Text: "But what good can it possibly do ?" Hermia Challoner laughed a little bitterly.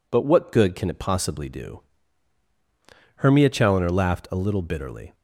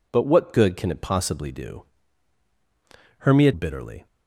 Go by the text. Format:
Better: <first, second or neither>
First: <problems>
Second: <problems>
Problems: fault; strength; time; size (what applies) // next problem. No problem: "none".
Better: first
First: none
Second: skips "Challoner laughed a little"; at 3.5 s